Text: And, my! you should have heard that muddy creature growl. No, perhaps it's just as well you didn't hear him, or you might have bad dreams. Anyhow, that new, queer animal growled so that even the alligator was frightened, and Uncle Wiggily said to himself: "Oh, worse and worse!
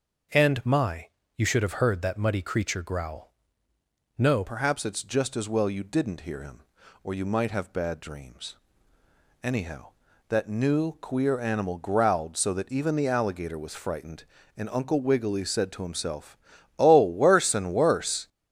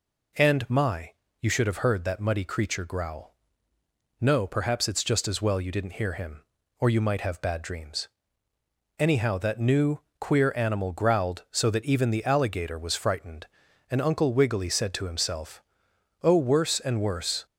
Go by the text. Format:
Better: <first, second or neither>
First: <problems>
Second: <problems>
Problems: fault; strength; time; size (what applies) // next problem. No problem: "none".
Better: second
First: starts louder than the rest; until 1.6 s; 6 dB // changes voice at "perhaps"; from 4.4 s on; 13.8 s long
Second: none